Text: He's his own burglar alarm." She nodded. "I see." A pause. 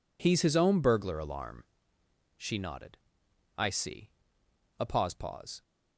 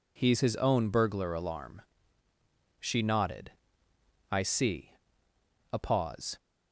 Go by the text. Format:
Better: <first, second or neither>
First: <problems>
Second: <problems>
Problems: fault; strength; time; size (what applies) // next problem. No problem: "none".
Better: second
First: says "pause" twice; at 5.1 s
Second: none